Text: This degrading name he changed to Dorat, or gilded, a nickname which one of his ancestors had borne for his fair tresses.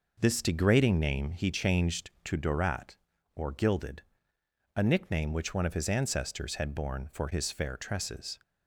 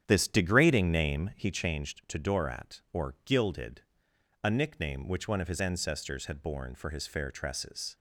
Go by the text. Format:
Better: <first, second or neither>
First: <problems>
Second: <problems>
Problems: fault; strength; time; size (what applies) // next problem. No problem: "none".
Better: first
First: none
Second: starts louder than the rest; strong; until 1.5 s; 9 dB